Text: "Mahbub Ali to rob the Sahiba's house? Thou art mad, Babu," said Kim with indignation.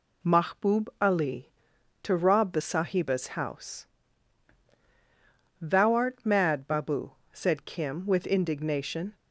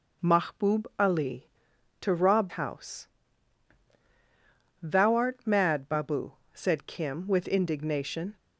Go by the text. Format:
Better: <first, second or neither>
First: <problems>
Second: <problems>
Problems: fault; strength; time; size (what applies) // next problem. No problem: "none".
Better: first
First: none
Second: skips "the Sahiba's"; at 2.4 s